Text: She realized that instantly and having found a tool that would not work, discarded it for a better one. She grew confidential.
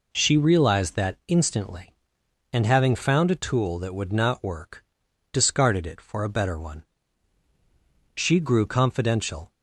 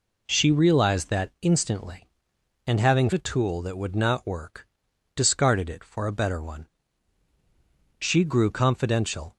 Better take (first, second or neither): first